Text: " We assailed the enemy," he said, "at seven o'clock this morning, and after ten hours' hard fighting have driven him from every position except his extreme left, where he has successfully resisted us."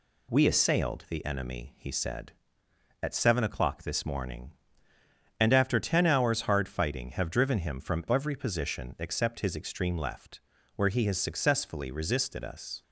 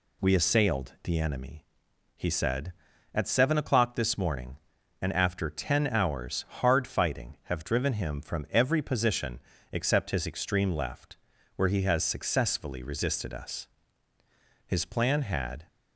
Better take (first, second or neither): first